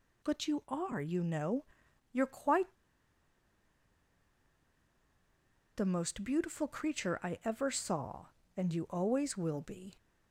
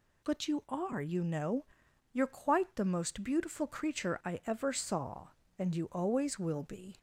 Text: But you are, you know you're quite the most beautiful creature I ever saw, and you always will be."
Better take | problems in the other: second | pauses between "know" and "you're"; noticeable; at 1.6 s; 0.48 s long; noticeable in the second // pauses between "quite" and "the"; strong; at 2.7 s; 3.0 s long

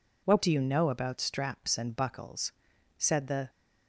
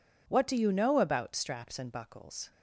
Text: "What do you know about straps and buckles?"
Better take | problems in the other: second | goes on to say "said the"; from 2.9 s on; 0.52 s long

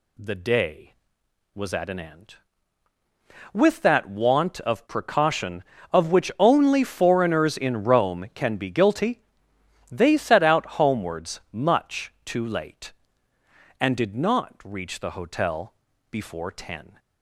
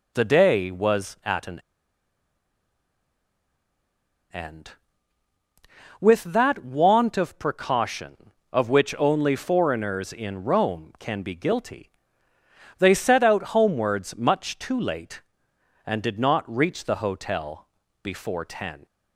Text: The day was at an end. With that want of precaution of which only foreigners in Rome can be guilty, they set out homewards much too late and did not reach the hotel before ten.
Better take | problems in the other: first | pauses between "an" and "end"; strong; at 1.6 s; 2.7 s long // pauses between "hotel" and "before"; slight; at 17.6 s; 0.34 s long; also in the first

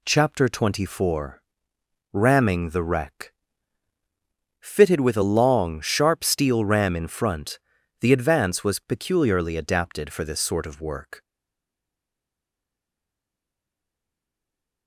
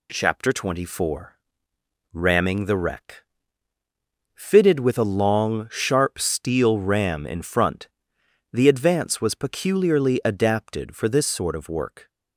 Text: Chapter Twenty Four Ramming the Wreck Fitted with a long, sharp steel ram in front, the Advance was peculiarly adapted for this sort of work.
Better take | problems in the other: second | pauses between "Four" and "Ramming"; noticeable; at 1.4 s; 0.72 s long; noticeable in the second // pauses between "Wreck" and "Fitted"; strong; at 3.3 s; 1.2 s long; also in the second // stays silent after the last word; strong; from 11.2 s on; 3.6 s long

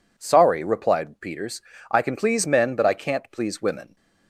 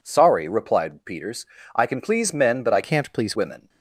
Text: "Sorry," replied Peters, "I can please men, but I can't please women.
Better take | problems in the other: first | changes voice from "can't" to "please"; from 2.8 to 3.3 s; 0.5 s long

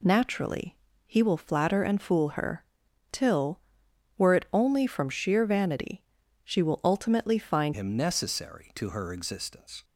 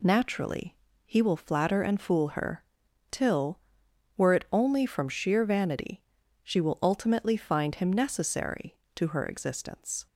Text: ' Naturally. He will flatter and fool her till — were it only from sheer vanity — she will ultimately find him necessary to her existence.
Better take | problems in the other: second | pauses between "her" and "till"; noticeable; at 2.6 s; 0.48 s long; noticeable in the second // changes voice at "him"; from 7.7 s on; 2.1 s long

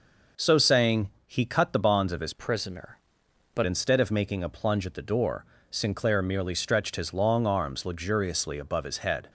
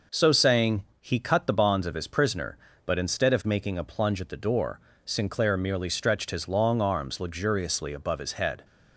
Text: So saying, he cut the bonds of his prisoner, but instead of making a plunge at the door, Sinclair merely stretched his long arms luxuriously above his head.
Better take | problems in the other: second | changes voice from "prisoner" to "but"; from 2.3 to 3.6 s; 1.3 s long

